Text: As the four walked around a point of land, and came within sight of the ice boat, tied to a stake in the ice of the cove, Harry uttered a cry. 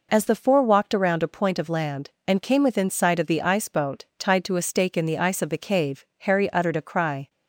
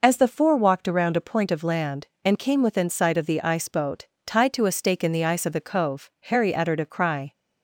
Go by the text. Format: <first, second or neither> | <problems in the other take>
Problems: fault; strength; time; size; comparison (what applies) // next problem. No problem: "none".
second | says "cave" for "cove"; at 5.5 s